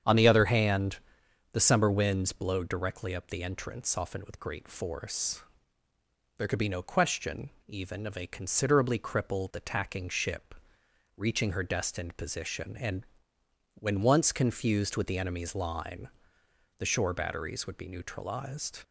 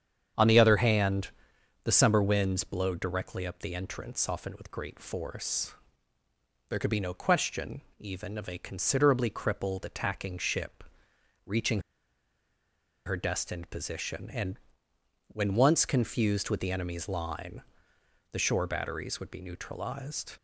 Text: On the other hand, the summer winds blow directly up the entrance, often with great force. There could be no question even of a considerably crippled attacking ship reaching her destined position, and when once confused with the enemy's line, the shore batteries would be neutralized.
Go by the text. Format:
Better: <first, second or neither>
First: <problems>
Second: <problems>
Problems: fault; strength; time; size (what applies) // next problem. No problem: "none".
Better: first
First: starts louder than the rest; strong; until 1.6 s; 8 dB // pauses between "question" and "even"; slight; at 7.5 s; 0.16 s long // pauses between "ship" and "reaching"; noticeable; at 10.5 s; 0.60 s long // pauses between "and" and "when"; noticeable; at 13.0 s; 0.70 s long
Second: starts louder than the rest; strong; until 1.9 s; 8 dB // pauses between "question" and "even"; slight; at 7.8 s; 0.16 s long // pauses between "ship" and "reaching"; noticeable; at 10.8 s; 0.60 s long // pauses between "reaching" and "her"; strong; at 11.7 s; 1.2 s long // pauses between "and" and "when"; noticeable; at 14.5 s; 0.70 s long